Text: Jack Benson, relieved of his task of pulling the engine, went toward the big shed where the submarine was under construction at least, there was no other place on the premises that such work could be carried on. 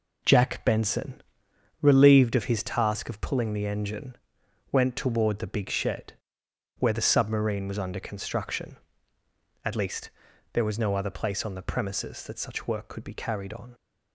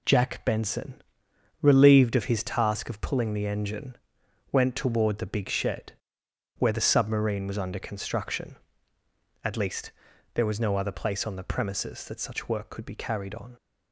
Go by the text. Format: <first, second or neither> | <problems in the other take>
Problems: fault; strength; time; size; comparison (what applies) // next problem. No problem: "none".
second | starts louder than the rest; until 1.8 s; 4 dB // pauses between "shed" and "where"; noticeable; at 6.1 s; 0.66 s long; noticeable in the second